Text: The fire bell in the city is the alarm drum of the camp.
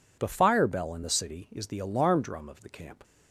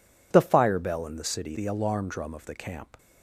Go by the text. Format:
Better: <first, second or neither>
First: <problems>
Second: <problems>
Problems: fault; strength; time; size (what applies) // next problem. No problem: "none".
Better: first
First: none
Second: skips "is"; at 1.5 s